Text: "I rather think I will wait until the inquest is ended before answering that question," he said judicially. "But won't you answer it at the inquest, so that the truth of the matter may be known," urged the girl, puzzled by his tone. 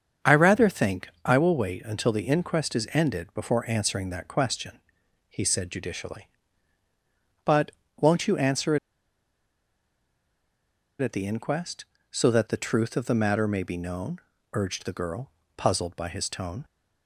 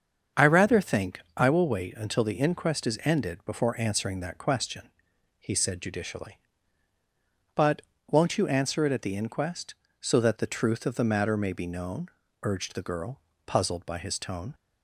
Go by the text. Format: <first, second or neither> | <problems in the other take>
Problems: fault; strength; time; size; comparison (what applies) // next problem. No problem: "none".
second | starts louder than the rest; strong; until 1.4 s; 7 dB; strong in the second // pauses between "think" and "I"; slight; at 1.0 s; 0.18 s long; slight in the second // pauses between "But" and "won't"; slight; at 7.7 s; 0.28 s long; slight in the second // pauses between "answer" and "it"; strong; at 8.7 s; 2.2 s long